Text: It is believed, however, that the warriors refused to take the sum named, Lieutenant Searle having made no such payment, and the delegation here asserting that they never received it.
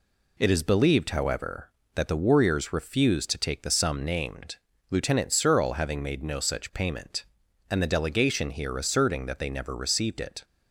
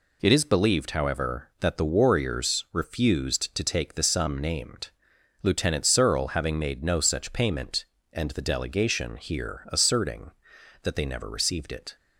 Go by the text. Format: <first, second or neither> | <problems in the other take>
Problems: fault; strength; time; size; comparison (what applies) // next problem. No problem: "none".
neither | none